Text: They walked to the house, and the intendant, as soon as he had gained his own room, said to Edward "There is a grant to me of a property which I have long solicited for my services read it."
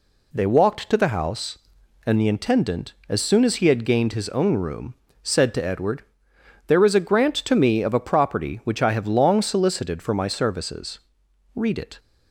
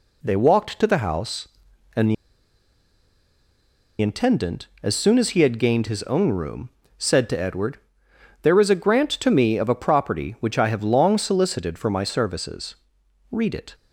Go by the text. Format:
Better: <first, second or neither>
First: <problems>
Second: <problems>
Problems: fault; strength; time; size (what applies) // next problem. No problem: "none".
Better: first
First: pauses between "Edward" and "There"; noticeable; at 6.0 s; 0.66 s long // pauses between "services" and "read"; noticeable; at 10.9 s; 0.56 s long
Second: pauses between "the" and "intendant"; strong; at 2.1 s; 1.8 s long // pauses between "Edward" and "There"; noticeable; at 7.7 s; 0.66 s long // pauses between "services" and "read"; noticeable; at 12.7 s; 0.56 s long